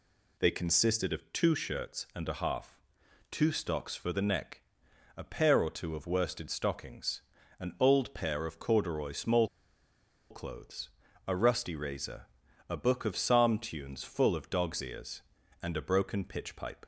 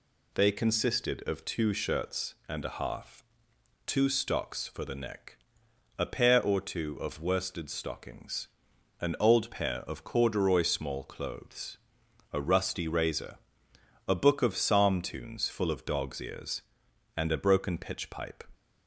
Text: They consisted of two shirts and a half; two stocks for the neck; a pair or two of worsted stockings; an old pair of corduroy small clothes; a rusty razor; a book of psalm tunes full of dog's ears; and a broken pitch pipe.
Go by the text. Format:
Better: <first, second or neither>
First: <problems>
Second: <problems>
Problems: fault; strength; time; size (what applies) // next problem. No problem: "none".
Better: second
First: pauses between "small" and "clothes"; noticeable; at 9.4 s; 0.83 s long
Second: none